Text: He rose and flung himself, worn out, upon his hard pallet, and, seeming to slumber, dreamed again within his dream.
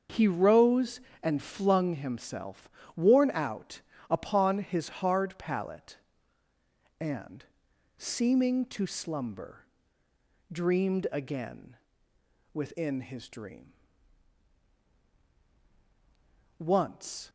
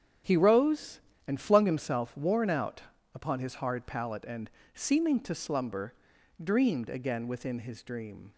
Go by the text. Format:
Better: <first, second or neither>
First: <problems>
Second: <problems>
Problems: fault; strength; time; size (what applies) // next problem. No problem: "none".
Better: second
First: starts louder than the rest; until 1.3 s; 6.5 dB // pauses between "again" and "within"; noticeable; at 11.7 s; 0.82 s long // goes on to say "Once"; noticeable; from 16.5 s on; 0.72 s long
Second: starts louder than the rest; strong; until 1.5 s; 8 dB